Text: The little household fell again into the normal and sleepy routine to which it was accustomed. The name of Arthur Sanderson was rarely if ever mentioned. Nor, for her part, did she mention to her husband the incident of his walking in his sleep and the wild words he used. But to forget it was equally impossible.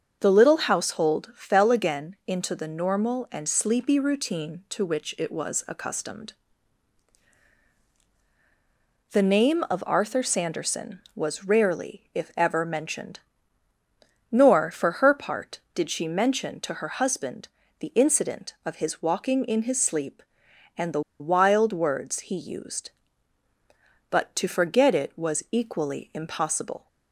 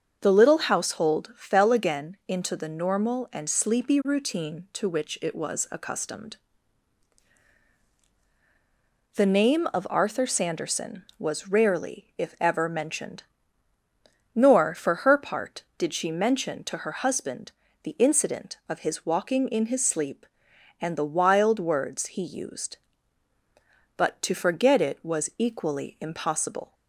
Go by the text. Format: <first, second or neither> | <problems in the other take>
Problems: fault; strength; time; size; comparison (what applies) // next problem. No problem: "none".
second | starts louder than the rest; until 1.2 s; 6.5 dB; also in the second // pauses between "husband" and "the"; slight; at 17.4 s; 0.32 s long; slight in the second // pauses between "the" and "wild"; slight; at 21.0 s; 0.19 s long